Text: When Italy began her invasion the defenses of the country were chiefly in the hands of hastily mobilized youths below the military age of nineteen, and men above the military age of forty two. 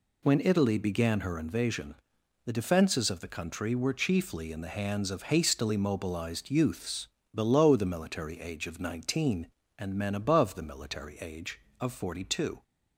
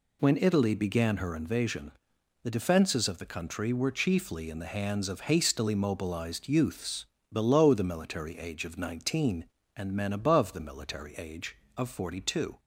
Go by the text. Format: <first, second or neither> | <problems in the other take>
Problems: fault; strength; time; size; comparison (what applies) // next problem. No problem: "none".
neither | pauses between "invasion" and "the"; noticeable; the same in both // pauses between "youths" and "below"; slight; the same in both